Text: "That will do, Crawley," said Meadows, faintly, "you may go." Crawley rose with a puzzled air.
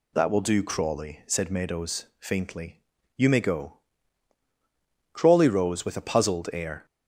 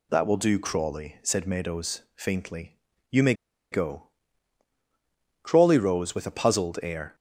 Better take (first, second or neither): first